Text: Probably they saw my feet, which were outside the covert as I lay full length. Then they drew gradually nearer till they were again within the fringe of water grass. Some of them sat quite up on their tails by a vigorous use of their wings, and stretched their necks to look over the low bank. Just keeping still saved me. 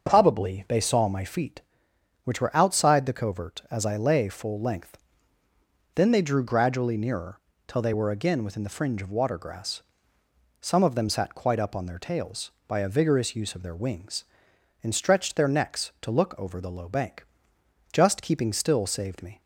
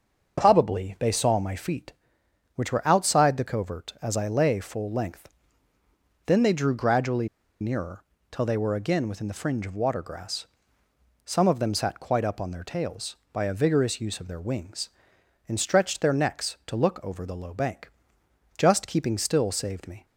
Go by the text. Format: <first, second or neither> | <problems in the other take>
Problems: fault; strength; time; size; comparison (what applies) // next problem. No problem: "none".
first | starts louder than the rest; until 1.4 s; 6.5 dB; also in the first // pauses between "gradually" and "nearer"; slight; at 7.2 s; 0.34 s long // pauses between "nearer" and "till"; slight; at 8.0 s; 0.28 s long; slight in the first